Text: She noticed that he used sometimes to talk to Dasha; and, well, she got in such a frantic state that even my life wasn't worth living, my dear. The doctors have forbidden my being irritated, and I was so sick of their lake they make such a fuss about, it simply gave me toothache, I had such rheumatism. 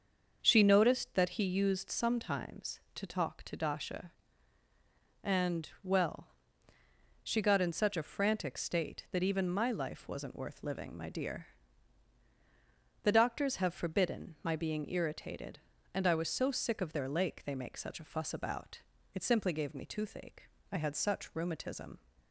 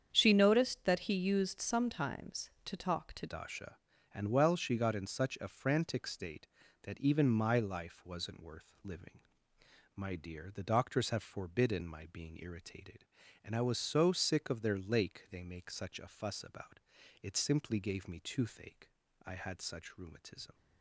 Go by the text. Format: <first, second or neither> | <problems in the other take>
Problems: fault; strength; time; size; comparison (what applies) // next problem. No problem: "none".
first | starts louder than the rest; strong; until 1.1 s; 8 dB; also in the first // changes voice at "Dasha"; from 3.2 s on; 17.3 s long